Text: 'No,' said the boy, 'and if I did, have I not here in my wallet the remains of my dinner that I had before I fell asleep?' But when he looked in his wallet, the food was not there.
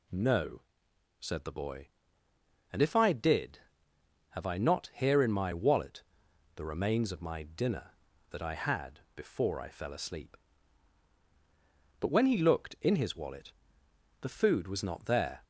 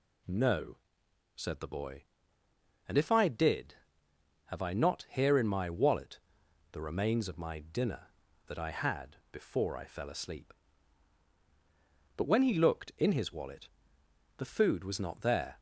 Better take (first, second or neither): neither